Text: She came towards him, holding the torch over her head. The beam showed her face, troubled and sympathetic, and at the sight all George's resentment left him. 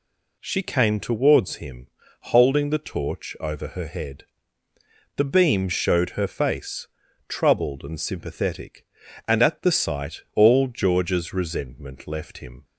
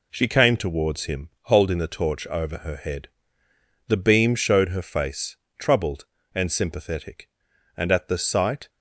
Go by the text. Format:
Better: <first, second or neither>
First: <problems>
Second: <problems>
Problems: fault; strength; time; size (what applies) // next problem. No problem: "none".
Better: first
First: none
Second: stops before "all George's resentment left him"; at 8.6 s